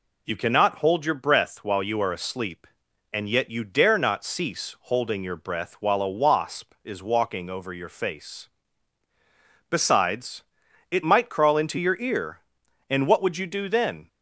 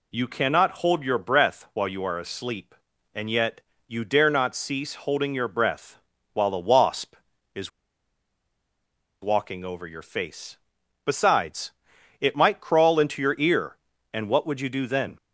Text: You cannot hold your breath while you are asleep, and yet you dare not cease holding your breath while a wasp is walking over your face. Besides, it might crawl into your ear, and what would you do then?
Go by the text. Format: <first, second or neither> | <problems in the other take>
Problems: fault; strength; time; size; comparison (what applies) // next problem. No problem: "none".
first | pauses between "yet" and "you"; slight; at 3.6 s; 0.26 s long // pauses between "breath" and "while"; at 5.9 s; 0.38 s long // pauses between "is" and "walking"; strong; at 7.7 s; 1.5 s long